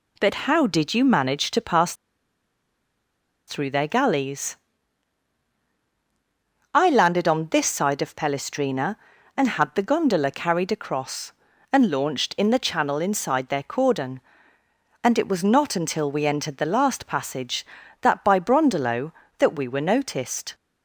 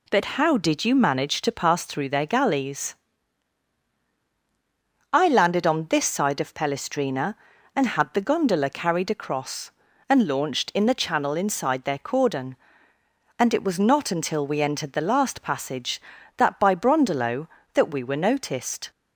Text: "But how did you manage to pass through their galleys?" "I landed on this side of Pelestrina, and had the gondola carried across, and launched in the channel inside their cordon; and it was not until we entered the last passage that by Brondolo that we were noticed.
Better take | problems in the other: second | pauses between "pass" and "through"; strong; at 1.9 s; 1.5 s long

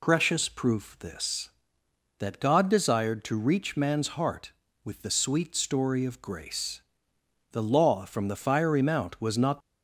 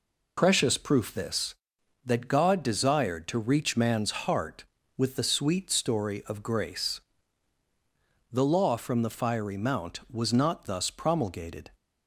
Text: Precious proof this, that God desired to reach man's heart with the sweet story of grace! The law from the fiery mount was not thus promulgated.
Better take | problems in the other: second | stops before "thus promulgated"; at 9.6 s

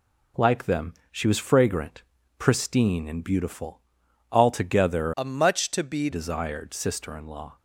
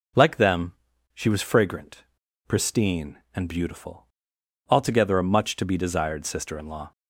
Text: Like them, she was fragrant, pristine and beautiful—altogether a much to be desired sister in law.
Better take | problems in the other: second | changes voice from "a" to "be"; from 5.1 to 6.0 s; 0.9 s long

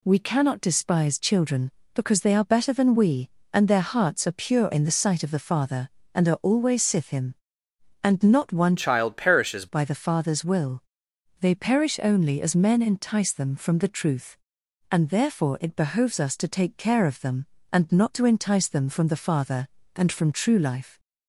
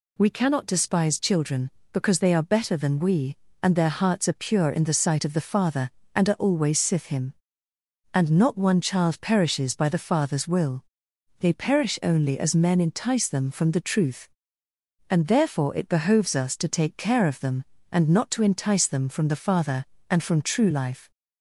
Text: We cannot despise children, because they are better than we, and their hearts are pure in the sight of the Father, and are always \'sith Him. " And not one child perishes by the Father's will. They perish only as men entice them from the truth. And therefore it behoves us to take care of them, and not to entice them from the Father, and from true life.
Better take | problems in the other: second | changes voice from "child" to "perishes"; from 8.7 to 9.6 s; 0.9 s long

